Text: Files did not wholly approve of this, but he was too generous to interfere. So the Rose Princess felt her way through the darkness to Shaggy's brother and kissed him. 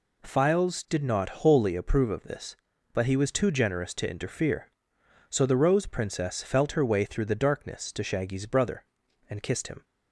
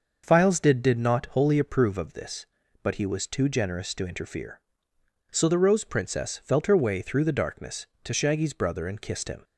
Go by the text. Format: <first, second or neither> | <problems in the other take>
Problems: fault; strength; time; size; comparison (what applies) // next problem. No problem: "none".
first | starts louder than the rest; until 1.2 s; 6 dB // says "did" twice; at 0.8 s